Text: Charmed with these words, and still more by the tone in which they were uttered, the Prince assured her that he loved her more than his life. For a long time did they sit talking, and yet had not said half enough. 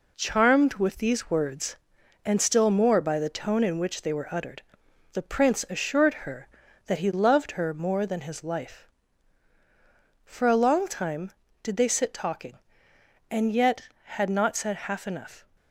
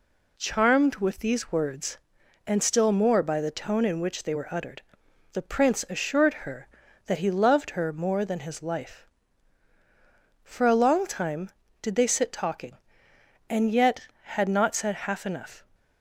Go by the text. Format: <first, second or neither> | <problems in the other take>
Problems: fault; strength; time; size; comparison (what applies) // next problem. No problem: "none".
second | gets quieter; noticeable; throughout; 5.5 dB